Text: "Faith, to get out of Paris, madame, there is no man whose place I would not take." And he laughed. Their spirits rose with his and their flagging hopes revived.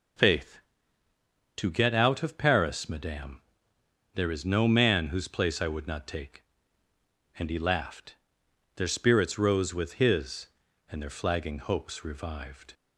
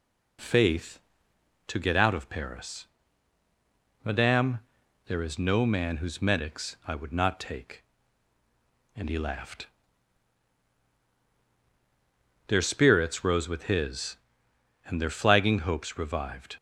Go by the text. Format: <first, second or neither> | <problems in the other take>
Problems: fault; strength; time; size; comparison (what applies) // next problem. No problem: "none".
first | says "medics" for "place"; at 6.2 s